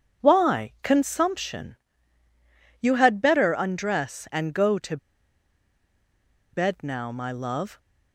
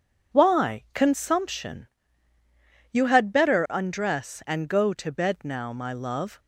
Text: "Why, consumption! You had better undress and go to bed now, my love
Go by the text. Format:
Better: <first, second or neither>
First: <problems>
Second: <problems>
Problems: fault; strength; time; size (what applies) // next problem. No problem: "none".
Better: second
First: pauses between "to" and "bed"; strong; at 4.9 s; 1.5 s long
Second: none